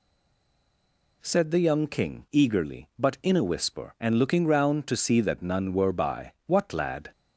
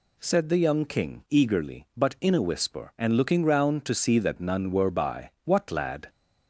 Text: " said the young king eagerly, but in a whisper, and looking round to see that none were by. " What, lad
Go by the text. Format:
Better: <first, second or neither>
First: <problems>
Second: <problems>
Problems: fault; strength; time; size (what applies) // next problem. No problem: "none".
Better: second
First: stays silent before the first word; noticeable; until 1.2 s; 1.2 s long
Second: none